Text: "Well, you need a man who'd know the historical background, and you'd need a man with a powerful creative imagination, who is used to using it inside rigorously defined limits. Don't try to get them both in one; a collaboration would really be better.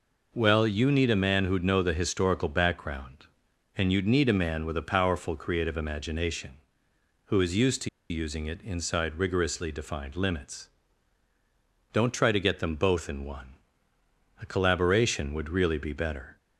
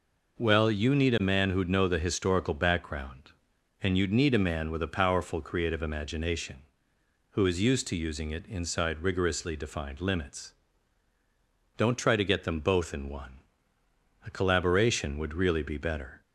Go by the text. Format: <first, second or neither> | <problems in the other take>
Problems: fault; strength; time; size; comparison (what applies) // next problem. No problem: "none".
second | pauses between "to" and "using"; slight; at 7.8 s; 0.21 s long